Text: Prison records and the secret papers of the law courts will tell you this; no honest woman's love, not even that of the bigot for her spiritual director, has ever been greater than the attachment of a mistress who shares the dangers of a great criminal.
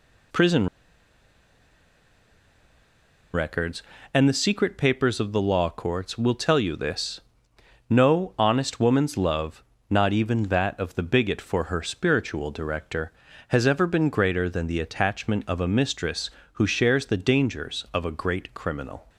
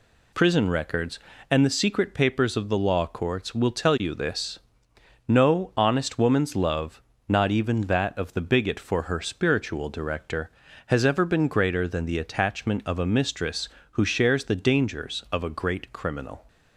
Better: second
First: pauses between "Prison" and "records"; strong; at 0.6 s; 2.6 s long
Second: none

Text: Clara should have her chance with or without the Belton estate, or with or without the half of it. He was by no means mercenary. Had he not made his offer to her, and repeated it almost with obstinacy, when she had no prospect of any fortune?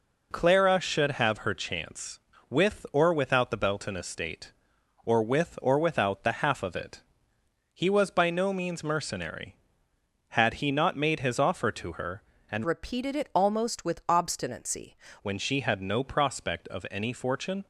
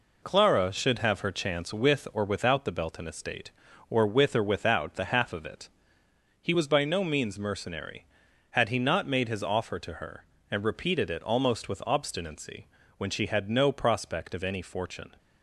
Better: second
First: changes voice from "repeated" to "obstinacy"; from 12.6 to 14.9 s; 2.3 s long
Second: none

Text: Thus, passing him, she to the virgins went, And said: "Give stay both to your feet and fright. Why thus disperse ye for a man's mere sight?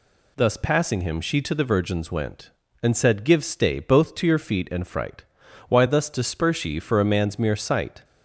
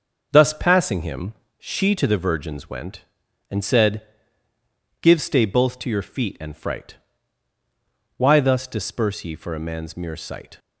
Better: neither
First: none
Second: none

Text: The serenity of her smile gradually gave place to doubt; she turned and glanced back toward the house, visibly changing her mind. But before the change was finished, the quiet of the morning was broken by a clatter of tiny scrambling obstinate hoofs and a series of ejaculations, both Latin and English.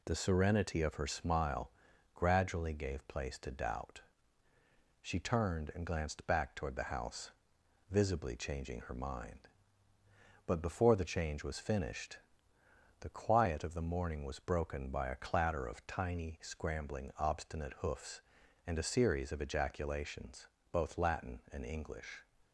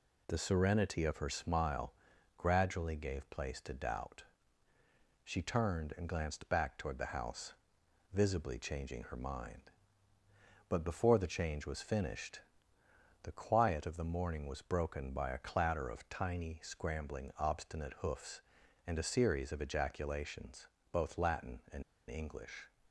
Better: first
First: pauses between "smile" and "gradually"; at 1.7 s; 0.42 s long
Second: pauses between "smile" and "gradually"; at 1.9 s; 0.42 s long // pauses between "and" and "English"; slight; at 21.8 s; 0.26 s long

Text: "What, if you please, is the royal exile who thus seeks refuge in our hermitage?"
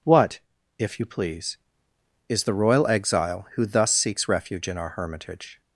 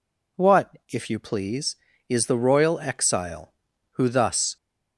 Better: first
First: none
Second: stops before "seeks refuge in our hermitage"; at 4.5 s

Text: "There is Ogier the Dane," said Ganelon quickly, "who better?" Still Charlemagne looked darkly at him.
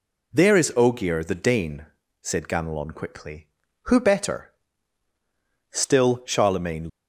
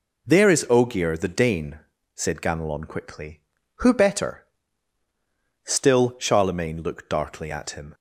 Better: second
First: stops before "looked darkly at him"; at 6.8 s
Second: none

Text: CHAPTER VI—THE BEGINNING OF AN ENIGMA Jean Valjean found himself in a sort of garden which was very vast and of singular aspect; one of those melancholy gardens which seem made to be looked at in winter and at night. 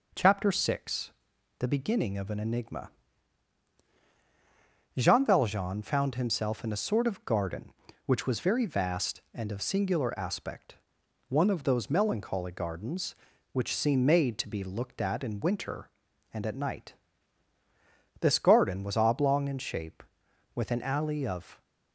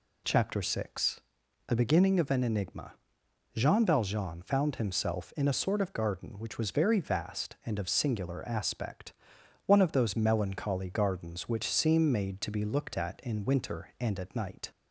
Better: second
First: pauses between "ENIGMA" and "Jean"; strong; at 2.8 s; 2.0 s long // goes on to say "This garden was oblong in shape with an alley of"; strong; from 18.1 s on; 3.4 s long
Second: pauses between "ENIGMA" and "Jean"; noticeable; at 2.9 s; 0.60 s long

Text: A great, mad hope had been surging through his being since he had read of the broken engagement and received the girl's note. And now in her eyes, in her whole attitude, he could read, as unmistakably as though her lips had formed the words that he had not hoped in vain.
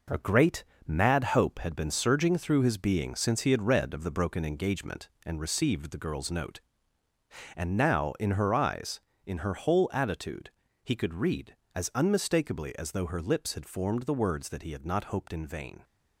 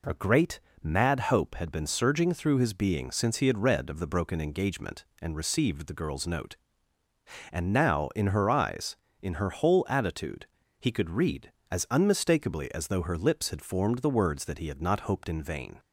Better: second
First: gets quieter; throughout; 6.5 dB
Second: none

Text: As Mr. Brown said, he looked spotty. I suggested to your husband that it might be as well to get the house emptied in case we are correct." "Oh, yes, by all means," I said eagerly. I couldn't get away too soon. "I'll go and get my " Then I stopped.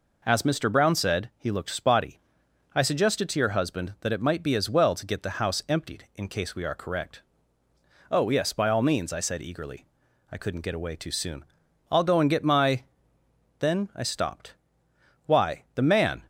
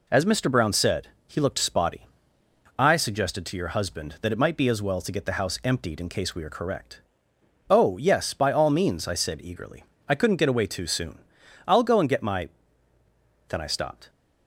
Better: second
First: goes on to say "Why the man"; noticeable; from 15.2 s on; 0.98 s long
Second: none

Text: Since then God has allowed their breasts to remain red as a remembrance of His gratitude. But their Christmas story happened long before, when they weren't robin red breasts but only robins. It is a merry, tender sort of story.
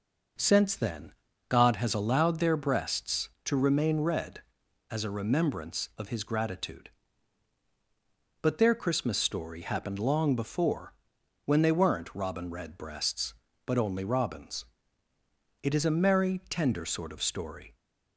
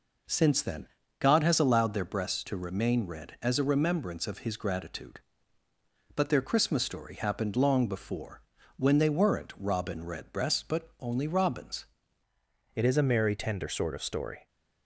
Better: first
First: pauses between "then" and "God"; slight; at 1.1 s; 0.36 s long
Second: pauses between "then" and "God"; slight; at 0.8 s; 0.32 s long // changes voice at "It"; from 12.7 s on; 1.7 s long

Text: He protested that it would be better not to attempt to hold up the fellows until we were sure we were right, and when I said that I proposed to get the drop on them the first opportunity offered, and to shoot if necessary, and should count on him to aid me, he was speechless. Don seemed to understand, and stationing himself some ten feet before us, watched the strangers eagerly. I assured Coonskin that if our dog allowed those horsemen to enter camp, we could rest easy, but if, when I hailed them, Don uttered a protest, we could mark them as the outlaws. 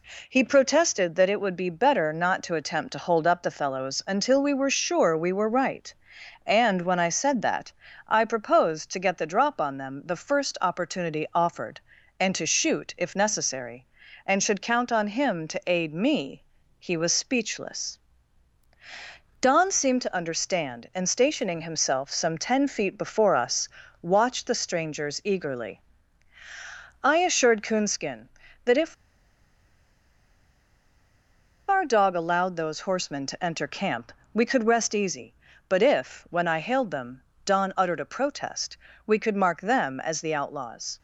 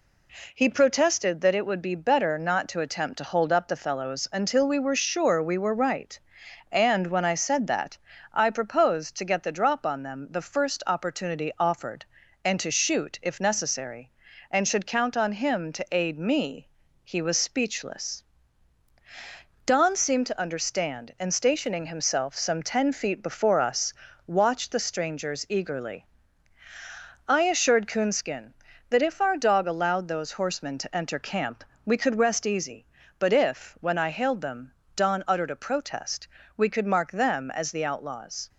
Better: second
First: pauses between "that" and "I"; slight; at 7.7 s; 0.36 s long // pauses between "if" and "our"; strong; at 28.9 s; 2.7 s long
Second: pauses between "that" and "I"; slight; at 7.9 s; 0.36 s long

